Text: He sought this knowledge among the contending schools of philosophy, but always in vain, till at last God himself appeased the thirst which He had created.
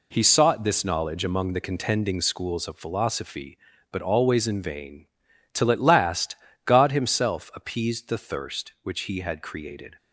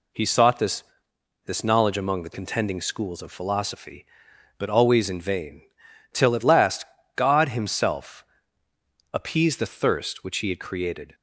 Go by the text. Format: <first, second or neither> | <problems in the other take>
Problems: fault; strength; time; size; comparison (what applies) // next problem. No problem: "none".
first | says "this" twice; at 1.4 s // pauses between "last" and "God"; slight; at 6.8 s; 0.32 s long; slight in the first // pauses between "himself" and "appeased"; noticeable; at 8.2 s; 0.88 s long